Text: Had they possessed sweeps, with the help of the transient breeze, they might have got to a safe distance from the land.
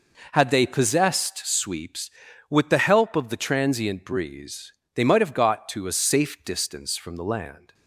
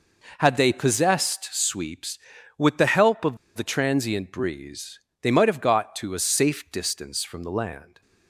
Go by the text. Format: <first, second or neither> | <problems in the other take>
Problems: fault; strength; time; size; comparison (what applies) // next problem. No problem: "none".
first | pauses between "of" and "the"; slight; at 3.3 s; 0.19 s long